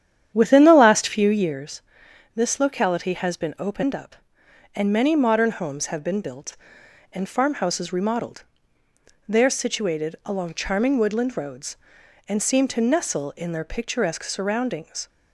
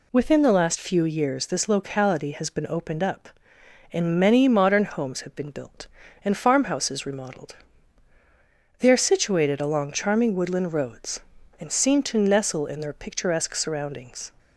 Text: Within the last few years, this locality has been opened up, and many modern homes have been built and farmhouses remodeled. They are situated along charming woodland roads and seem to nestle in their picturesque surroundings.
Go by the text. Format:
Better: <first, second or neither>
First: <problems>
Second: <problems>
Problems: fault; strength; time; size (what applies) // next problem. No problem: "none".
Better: second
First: starts louder than the rest; strong; until 1.5 s; 9.5 dB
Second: none